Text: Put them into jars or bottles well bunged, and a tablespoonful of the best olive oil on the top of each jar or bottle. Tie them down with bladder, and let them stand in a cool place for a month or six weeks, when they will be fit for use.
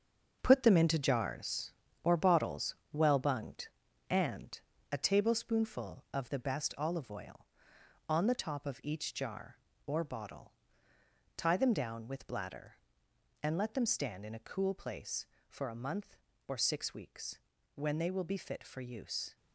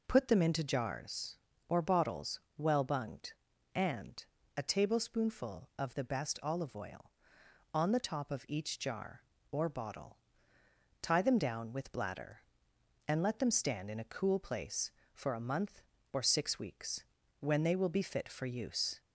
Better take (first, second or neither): second